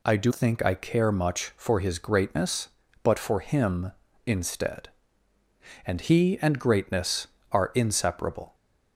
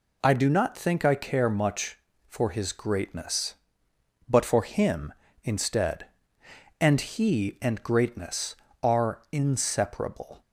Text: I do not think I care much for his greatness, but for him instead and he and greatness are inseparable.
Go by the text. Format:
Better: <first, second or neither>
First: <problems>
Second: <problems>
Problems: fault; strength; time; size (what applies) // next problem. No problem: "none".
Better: second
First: skips "not"; at 0.3 s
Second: none